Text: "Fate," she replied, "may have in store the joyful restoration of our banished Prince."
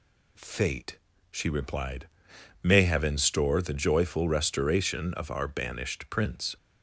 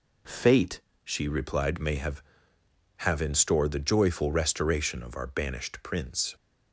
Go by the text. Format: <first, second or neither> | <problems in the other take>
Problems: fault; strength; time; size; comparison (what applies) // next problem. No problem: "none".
first | says "have" twice; at 2.9 s